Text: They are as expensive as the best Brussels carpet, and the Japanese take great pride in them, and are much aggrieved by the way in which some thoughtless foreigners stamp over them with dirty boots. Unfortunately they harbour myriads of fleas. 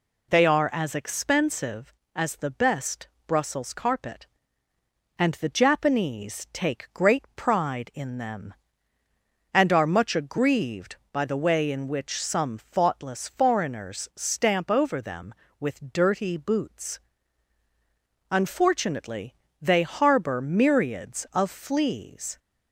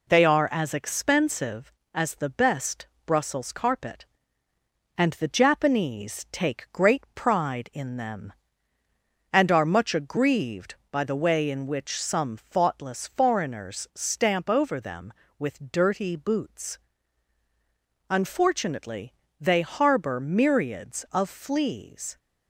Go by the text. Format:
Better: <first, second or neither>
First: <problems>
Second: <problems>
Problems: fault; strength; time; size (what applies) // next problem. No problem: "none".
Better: first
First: pauses between "best" and "Brussels"; slight; at 3.0 s; 0.18 s long // pauses between "Unfortunately" and "they"; slight; at 19.3 s; 0.26 s long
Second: gets quieter; slight; throughout; 2.5 dB // pauses between "best" and "Brussels"; slight; at 2.8 s; 0.18 s long // pauses between "Unfortunately" and "they"; slight; at 19.1 s; 0.26 s long